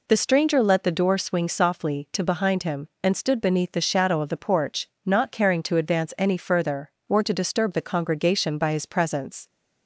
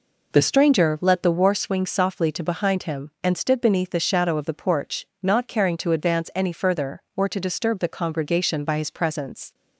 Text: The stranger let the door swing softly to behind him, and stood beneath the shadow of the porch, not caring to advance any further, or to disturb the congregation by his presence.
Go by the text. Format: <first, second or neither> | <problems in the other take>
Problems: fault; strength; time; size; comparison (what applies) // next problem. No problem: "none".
first | says "war" for "door"; at 1.3 s